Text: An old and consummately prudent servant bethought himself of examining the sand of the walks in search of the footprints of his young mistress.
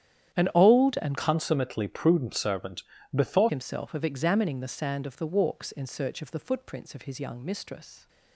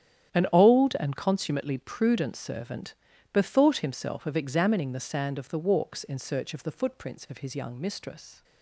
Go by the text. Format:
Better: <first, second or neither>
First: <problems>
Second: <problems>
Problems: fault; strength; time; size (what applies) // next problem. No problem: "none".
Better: second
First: starts louder than the rest; strong; until 1.4 s; 10 dB // changes voice from "consummately" to "bethought"; from 1.1 to 3.5 s; 2.4 s long // pauses between "servant" and "bethought"; slight; at 2.8 s; 0.30 s long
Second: starts louder than the rest; strong; until 1.4 s; 10 dB // pauses between "servant" and "bethought"; at 2.9 s; 0.38 s long